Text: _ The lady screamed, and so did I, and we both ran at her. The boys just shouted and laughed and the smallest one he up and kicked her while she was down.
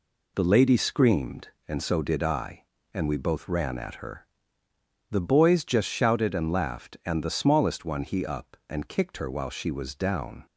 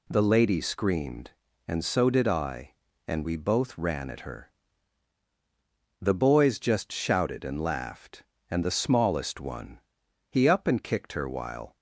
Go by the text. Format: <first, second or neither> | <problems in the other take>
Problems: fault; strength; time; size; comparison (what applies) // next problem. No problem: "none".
first | pauses between "one" and "he"; noticeable; at 9.8 s; 0.48 s long // stops before "she was down"; at 11.7 s